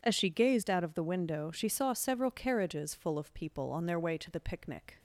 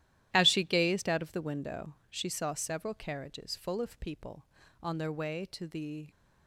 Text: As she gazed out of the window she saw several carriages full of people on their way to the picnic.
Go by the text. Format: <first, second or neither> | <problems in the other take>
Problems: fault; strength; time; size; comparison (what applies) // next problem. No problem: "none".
first | starts louder than the rest; strong; until 1.3 s; 13 dB // pauses between "window" and "she"; slight; at 1.9 s; 0.16 s long // stops before "picnic"; at 6.1 s